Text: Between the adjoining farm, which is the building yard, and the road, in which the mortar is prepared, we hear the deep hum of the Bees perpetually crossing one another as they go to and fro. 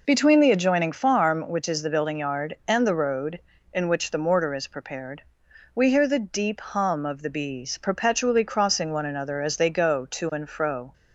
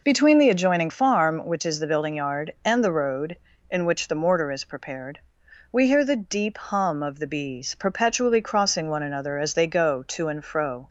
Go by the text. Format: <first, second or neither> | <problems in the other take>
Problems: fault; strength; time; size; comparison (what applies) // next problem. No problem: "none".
neither | none